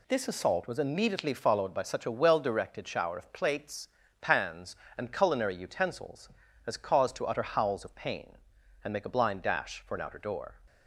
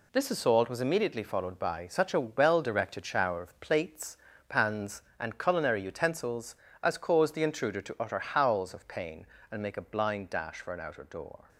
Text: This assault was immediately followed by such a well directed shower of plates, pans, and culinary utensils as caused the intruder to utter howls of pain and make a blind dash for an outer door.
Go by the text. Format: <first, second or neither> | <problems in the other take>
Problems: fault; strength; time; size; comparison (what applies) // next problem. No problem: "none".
second | skips "the intruder"; at 7.1 s